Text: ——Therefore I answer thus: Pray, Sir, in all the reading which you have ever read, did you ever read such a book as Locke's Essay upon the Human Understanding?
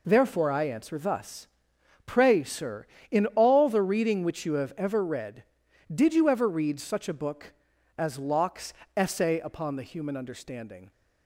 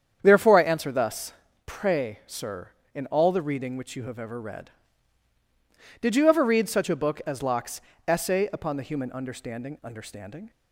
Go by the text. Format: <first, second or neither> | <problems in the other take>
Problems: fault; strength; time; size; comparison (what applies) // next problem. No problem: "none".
first | starts louder than the rest; strong; until 1.2 s; 8 dB // pauses between "Locke's" and "Essay"; slight; at 7.7 s; 0.26 s long; slight in the first // says "Understanding" twice; at 9.8 s